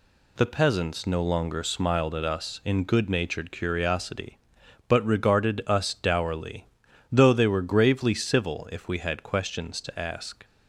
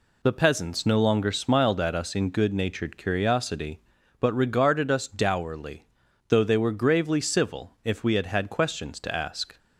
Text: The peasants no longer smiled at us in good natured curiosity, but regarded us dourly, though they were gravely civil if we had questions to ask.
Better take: first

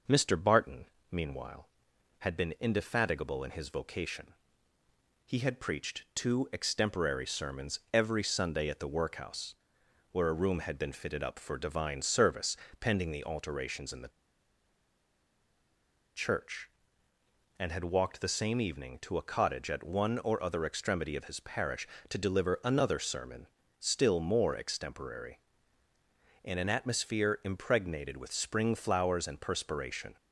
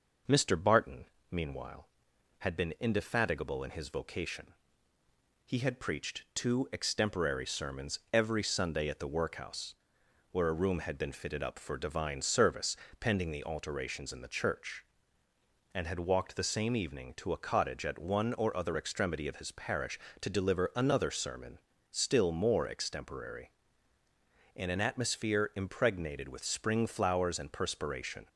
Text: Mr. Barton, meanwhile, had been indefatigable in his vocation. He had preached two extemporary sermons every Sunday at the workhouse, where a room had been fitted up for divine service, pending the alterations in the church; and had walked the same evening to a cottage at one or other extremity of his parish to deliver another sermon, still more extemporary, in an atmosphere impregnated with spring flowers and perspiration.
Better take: second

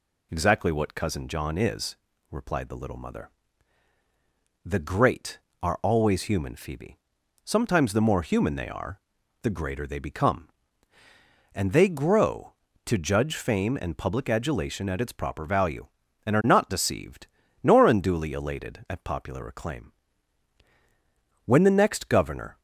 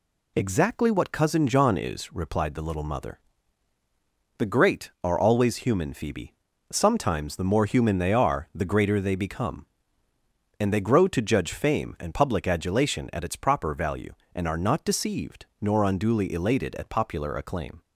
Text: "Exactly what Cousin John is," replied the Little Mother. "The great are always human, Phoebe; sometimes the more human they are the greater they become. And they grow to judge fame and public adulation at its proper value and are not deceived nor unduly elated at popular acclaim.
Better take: second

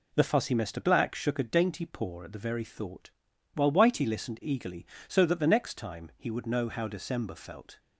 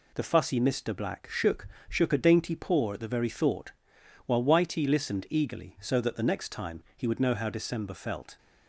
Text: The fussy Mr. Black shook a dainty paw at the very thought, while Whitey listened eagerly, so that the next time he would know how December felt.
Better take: first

